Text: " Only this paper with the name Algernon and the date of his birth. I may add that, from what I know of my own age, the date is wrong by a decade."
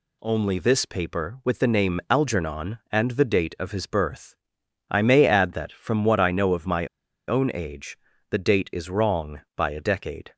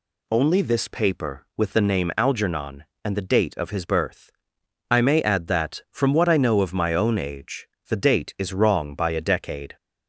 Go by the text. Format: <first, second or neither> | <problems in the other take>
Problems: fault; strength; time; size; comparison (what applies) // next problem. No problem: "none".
second | pauses between "my" and "own"; at 6.8 s; 0.41 s long